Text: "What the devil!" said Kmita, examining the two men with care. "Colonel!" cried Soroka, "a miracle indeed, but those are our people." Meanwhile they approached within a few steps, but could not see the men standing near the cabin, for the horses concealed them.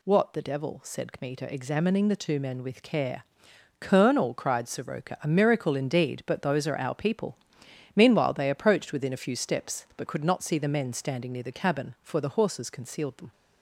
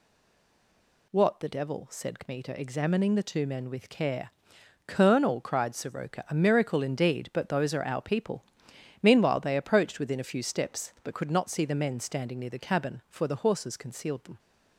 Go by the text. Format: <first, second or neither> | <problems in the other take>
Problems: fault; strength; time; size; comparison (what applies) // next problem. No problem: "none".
first | stays silent before the first word; until 1.1 s; 1.1 s long